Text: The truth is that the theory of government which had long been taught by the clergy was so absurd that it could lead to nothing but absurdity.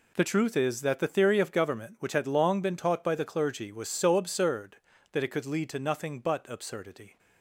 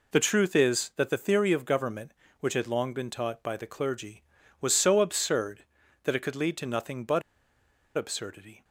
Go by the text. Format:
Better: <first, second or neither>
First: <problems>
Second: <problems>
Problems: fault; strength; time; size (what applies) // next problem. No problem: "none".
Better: first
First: none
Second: pauses between "but" and "absurdity"; noticeable; at 7.2 s; 0.76 s long